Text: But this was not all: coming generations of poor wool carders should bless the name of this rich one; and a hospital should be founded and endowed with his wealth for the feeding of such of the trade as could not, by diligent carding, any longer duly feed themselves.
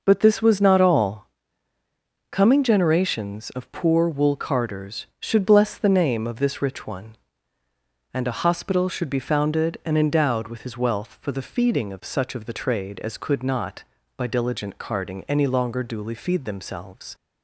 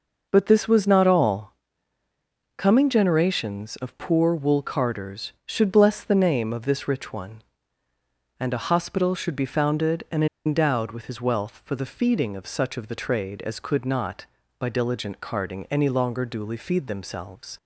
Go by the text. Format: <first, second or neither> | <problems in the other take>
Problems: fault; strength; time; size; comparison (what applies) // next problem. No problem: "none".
first | pauses between "and" and "endowed"; slight; at 10.2 s; 0.20 s long